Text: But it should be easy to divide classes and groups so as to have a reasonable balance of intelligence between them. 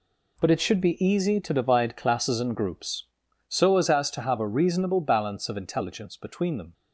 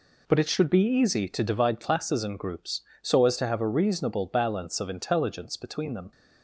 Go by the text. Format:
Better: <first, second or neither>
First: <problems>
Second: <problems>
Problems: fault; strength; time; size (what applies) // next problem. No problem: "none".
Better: second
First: says "as" twice; at 3.8 s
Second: none